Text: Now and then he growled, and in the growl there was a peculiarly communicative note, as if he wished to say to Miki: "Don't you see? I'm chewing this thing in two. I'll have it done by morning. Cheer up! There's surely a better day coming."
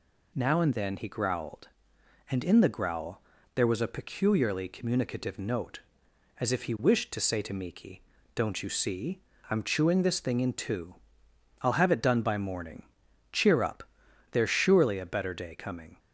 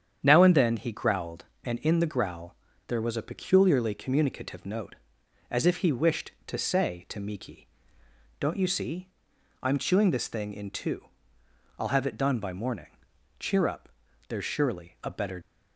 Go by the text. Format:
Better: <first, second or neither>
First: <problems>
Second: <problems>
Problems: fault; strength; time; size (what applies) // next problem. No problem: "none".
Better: first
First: pauses between "growl" and "there"; slight; at 3.2 s; 0.36 s long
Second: starts louder than the rest; strong; until 1.2 s; 8.5 dB // pauses between "growl" and "there"; slight; at 2.5 s; 0.32 s long // stops before "day coming"; at 15.4 s